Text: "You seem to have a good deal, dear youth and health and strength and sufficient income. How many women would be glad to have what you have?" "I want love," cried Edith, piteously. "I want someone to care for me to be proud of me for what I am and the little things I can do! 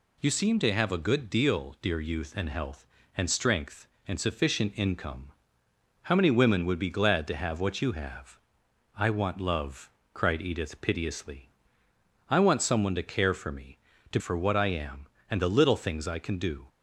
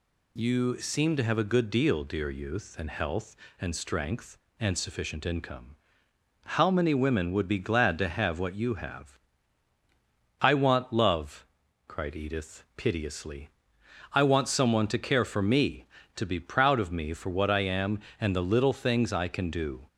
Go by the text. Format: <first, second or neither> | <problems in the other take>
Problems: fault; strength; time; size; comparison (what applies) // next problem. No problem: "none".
second | skips "be proud of me"; at 14.1 s